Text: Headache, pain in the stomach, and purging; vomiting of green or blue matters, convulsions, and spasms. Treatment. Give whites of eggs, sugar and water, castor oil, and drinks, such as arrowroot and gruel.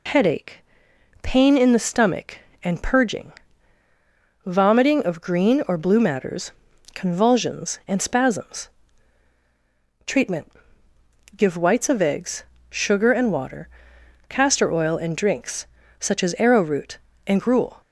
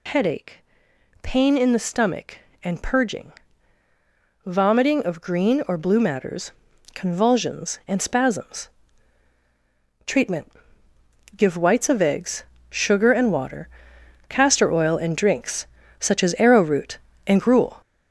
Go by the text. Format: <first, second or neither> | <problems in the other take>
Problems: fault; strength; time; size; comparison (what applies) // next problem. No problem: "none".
first | gets louder; noticeable; throughout; 5.5 dB